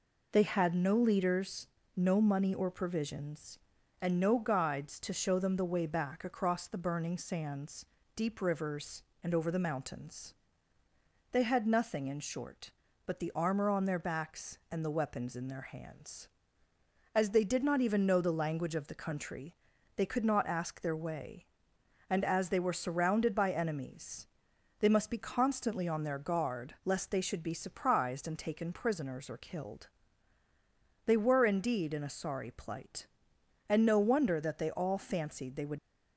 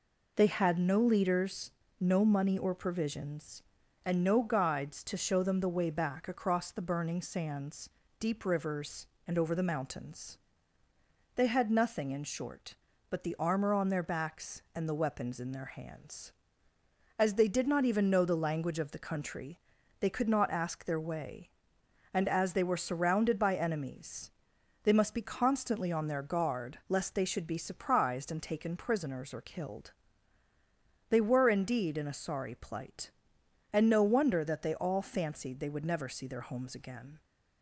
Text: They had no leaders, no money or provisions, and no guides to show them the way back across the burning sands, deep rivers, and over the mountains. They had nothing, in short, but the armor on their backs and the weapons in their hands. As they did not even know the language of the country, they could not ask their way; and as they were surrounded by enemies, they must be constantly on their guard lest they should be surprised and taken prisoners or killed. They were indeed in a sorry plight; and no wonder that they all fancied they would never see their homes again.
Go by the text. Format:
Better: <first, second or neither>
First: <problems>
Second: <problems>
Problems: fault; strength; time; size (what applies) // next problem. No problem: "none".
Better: second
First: stops before "never see their homes again"; at 35.7 s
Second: none